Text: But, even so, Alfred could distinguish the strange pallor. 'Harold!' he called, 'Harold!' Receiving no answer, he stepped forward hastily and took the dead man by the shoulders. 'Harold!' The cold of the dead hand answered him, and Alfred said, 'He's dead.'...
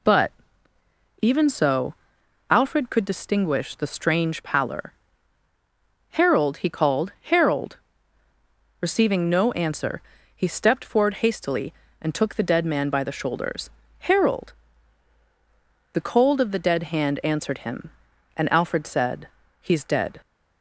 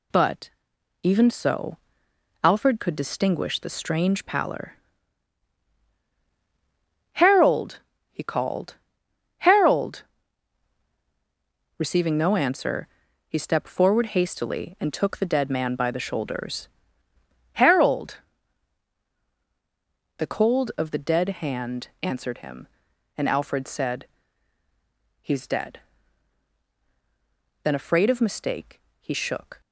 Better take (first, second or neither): first